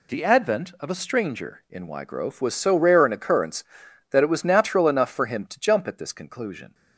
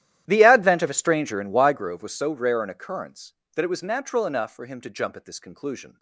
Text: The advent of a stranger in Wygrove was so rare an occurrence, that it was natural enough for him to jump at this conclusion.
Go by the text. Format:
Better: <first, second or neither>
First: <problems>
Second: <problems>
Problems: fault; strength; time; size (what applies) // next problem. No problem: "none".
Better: first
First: none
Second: starts louder than the rest; strong; until 1.9 s; 12.5 dB